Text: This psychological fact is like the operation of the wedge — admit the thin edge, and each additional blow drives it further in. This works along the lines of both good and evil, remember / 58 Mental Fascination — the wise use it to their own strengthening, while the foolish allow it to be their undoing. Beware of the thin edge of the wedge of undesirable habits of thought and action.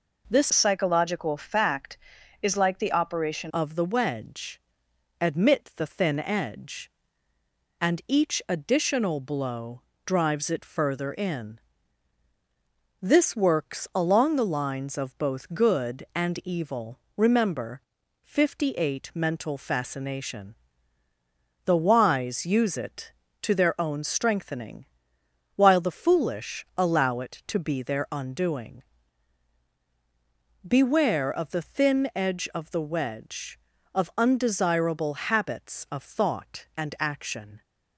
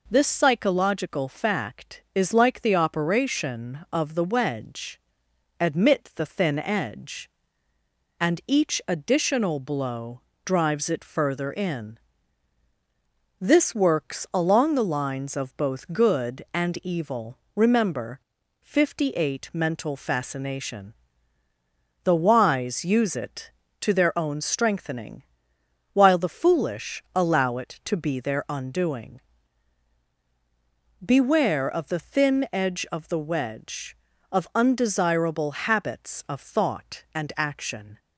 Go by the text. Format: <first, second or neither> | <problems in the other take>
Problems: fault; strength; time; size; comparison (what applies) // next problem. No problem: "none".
second | changes voice from "psychological" to "operation"; from 0.5 to 3.5 s; 3.0 s long // pauses between "blow" and "drives"; slight; at 9.8 s; 0.24 s long; slight in the second